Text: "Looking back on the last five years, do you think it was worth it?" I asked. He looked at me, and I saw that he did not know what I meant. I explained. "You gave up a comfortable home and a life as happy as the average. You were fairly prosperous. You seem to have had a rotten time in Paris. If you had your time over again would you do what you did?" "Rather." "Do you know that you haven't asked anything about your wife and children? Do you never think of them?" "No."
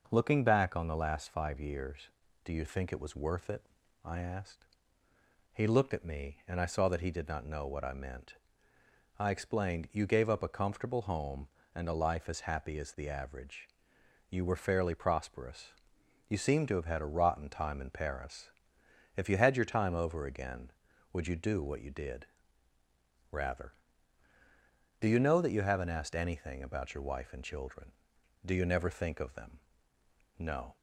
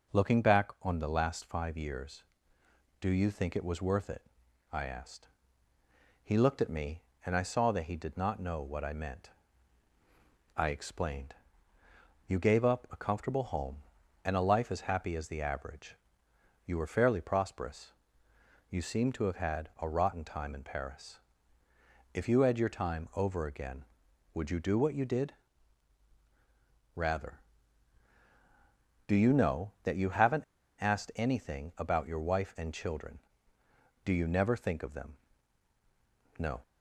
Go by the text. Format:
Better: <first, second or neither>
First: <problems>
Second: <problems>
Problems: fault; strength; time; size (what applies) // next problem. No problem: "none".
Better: first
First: none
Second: pauses between "haven't" and "asked"; slight; at 30.4 s; 0.35 s long